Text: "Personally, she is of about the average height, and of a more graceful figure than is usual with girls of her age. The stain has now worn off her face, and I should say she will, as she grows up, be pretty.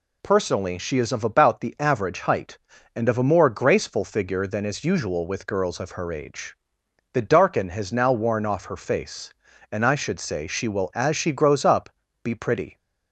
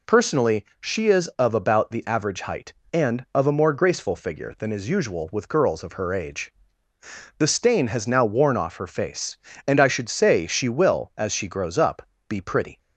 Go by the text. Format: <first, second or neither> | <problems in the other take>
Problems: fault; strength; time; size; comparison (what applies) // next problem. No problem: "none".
second | says "darken" for "stain"; at 7.2 s